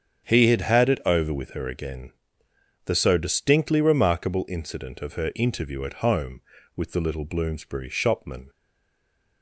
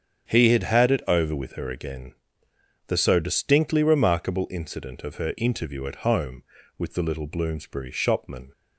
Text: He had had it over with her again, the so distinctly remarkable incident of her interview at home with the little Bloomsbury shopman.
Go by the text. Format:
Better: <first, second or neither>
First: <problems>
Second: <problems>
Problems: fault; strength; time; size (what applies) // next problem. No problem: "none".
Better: second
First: starts louder than the rest; strong; until 1.2 s; 8 dB // stays silent after the last word; slight; from 8.4 s on; 1.0 s long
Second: starts louder than the rest; strong; until 1.3 s; 8 dB